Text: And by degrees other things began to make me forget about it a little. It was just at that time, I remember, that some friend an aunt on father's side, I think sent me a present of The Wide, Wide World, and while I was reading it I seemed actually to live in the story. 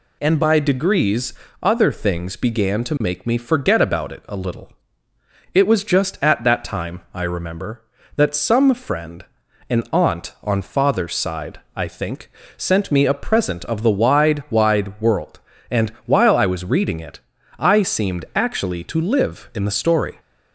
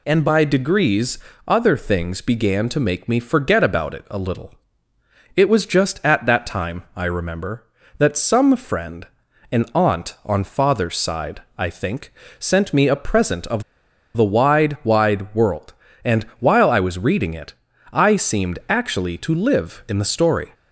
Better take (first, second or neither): first